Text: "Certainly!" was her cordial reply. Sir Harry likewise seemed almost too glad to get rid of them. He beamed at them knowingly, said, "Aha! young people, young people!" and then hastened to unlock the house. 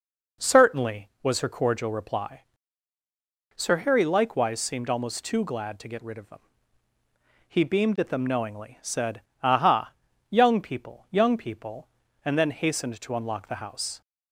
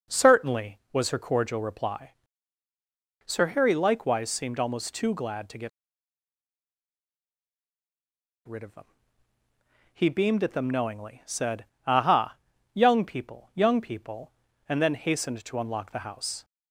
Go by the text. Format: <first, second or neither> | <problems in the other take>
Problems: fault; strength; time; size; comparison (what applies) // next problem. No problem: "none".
first | pauses between "get" and "rid"; strong; at 5.6 s; 2.7 s long